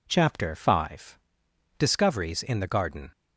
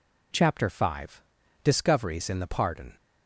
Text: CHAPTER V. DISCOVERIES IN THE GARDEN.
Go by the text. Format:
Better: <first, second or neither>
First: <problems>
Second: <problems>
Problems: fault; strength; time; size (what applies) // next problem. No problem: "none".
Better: first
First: none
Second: says "Pardon" for "GARDEN"; at 2.4 s